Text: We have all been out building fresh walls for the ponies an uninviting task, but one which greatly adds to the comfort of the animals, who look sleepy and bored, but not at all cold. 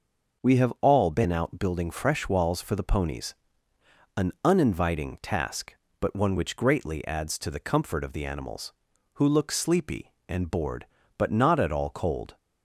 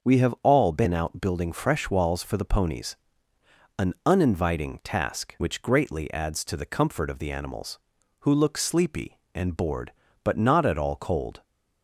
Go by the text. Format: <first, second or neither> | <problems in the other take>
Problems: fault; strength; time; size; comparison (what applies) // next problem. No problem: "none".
first | pauses between "ponies" and "an"; noticeable; at 2.9 s; 0.82 s long; noticeable in the first // skips "but one"; at 5.3 s